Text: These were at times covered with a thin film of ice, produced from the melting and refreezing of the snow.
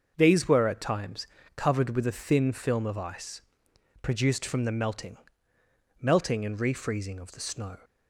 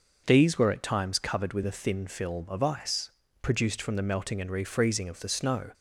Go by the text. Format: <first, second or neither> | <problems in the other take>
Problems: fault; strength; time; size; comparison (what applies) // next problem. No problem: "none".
second | starts louder than the rest; until 1.1 s; 6 dB // pauses between "times" and "covered"; slight; at 1.2 s; 0.30 s long // says "melting" twice; at 6.0 s